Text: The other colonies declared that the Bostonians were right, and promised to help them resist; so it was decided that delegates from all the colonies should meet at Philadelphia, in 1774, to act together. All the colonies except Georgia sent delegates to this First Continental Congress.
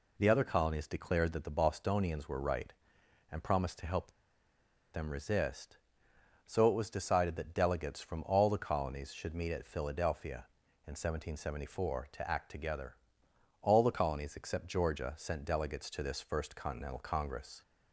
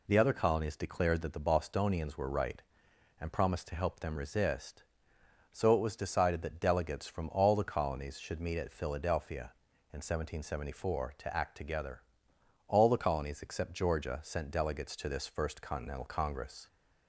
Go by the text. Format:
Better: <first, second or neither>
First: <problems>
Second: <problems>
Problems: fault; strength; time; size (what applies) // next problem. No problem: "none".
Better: second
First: pauses between "help" and "them"; noticeable; at 4.1 s; 0.81 s long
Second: none